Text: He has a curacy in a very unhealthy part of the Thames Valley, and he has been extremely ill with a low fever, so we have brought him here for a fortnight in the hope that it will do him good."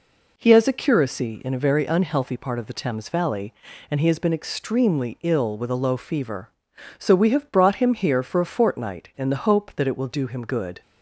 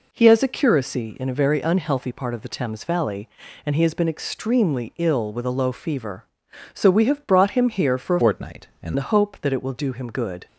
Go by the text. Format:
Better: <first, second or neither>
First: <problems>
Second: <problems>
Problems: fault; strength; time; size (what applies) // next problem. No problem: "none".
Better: first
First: none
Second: changes voice from "fortnight" to "in"; from 8.2 to 8.9 s; 0.7 s long